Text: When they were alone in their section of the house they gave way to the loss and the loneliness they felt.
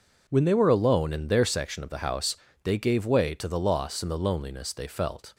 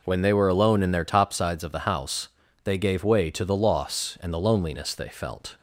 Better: first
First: pauses between "house" and "they"; slight; at 2.3 s; 0.30 s long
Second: says "topsides" for "section"; at 1.0 s // pauses between "house" and "they"; slight; at 2.2 s; 0.36 s long

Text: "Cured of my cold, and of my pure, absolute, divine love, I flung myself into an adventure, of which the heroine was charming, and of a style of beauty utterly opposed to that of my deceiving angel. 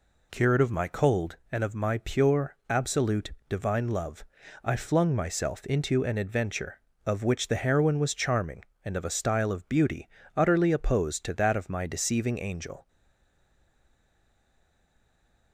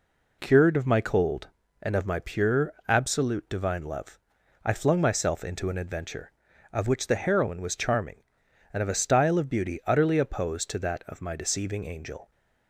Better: second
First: pauses between "beauty" and "utterly"; slight; at 10.0 s; 0.28 s long // stays silent after the last word; strong; from 12.8 s on; 2.7 s long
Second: none

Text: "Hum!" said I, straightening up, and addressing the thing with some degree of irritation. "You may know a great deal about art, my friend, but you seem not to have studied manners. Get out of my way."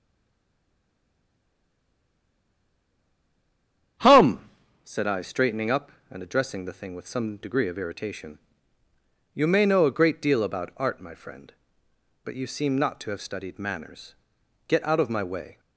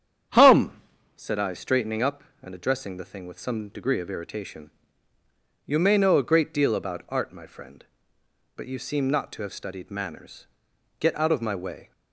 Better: second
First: stays silent before the first word; strong; until 3.9 s; 3.9 s long // starts louder than the rest; strong; until 5.3 s; 8.5 dB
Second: starts louder than the rest; strong; until 1.6 s; 8.5 dB

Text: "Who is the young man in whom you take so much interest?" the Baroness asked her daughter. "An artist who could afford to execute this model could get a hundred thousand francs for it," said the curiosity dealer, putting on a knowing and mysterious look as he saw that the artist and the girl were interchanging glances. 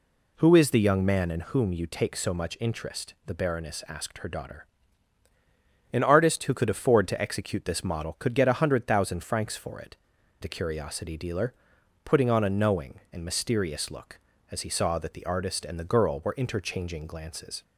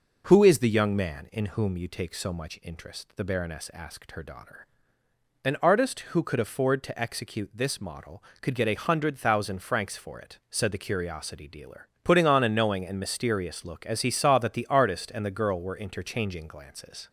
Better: second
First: skips "said"; at 10.1 s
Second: none

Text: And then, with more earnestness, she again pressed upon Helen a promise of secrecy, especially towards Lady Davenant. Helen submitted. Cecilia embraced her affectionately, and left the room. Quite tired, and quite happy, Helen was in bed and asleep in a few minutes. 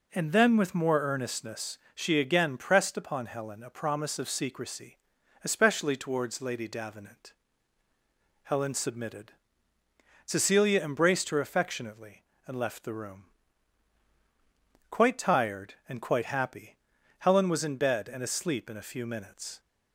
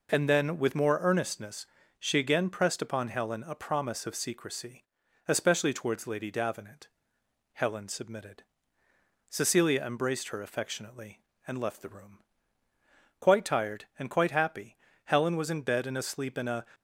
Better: first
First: none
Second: stops before "few minutes"; at 16.7 s

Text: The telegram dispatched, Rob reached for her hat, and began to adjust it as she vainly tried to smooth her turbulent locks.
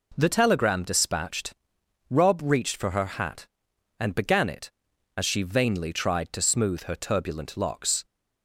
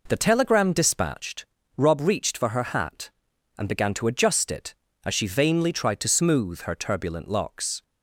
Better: second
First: skips "to adjust"; at 4.4 s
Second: none

